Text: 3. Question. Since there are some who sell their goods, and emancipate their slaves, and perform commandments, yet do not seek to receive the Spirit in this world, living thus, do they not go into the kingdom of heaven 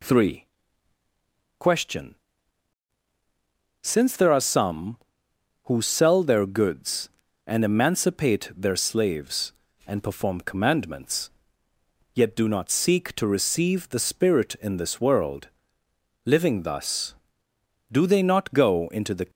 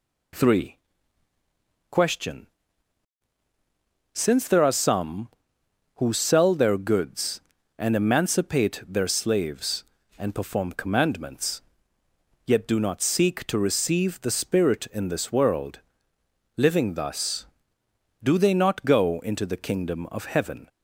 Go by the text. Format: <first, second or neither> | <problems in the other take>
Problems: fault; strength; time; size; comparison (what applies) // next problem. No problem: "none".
second | stops before "kingdom of heaven"; at 19.3 s